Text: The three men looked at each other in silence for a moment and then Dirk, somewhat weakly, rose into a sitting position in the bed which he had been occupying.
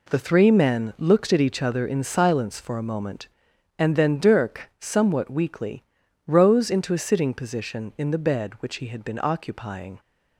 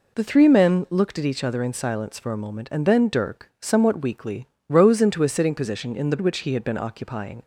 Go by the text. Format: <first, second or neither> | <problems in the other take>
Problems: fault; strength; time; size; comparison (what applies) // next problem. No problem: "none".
first | skips "bed"; at 6.1 s